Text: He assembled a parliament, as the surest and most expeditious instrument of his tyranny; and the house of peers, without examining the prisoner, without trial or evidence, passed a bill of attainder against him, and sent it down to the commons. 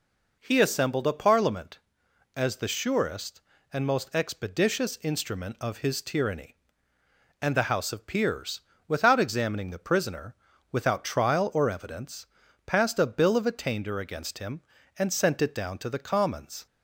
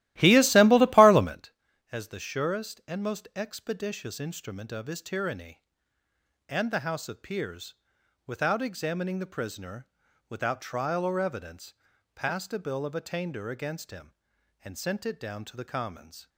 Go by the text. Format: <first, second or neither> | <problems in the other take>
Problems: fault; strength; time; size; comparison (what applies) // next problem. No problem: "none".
first | starts louder than the rest; strong; until 1.4 s; 15.5 dB